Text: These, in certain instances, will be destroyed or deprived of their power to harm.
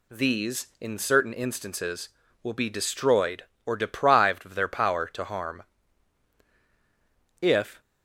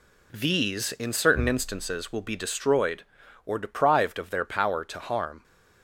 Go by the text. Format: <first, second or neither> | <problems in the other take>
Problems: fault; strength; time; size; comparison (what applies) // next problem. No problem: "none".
second | goes on to say "If"; slight; from 7.4 s on; 0.40 s long